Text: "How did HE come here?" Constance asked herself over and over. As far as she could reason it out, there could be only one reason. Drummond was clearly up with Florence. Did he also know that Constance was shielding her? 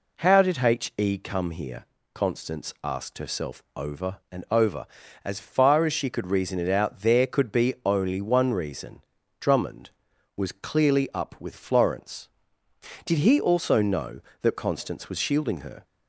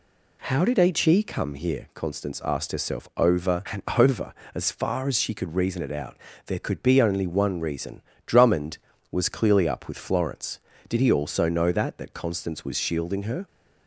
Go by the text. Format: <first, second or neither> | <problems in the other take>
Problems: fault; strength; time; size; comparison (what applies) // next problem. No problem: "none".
first | pauses between "and" and "over"; slight; at 3.8 s; 0.16 s long // says "that" twice; at 11.9 s